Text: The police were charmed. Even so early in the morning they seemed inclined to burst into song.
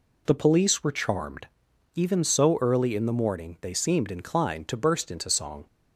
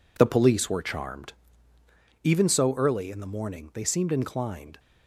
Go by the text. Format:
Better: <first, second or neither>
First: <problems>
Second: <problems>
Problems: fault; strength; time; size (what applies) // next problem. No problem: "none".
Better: first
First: none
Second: stops before "to burst into song"; at 4.7 s